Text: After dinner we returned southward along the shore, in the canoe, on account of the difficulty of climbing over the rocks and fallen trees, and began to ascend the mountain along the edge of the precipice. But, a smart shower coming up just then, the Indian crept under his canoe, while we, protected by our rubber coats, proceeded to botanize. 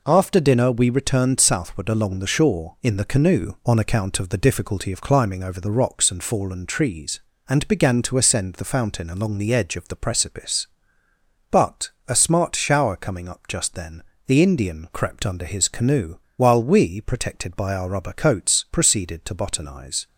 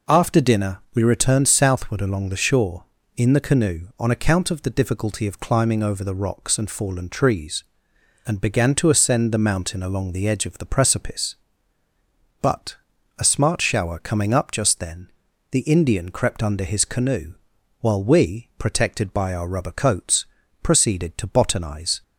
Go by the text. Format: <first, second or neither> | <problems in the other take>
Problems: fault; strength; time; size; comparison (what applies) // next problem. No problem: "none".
second | says "fountain" for "mountain"; at 8.6 s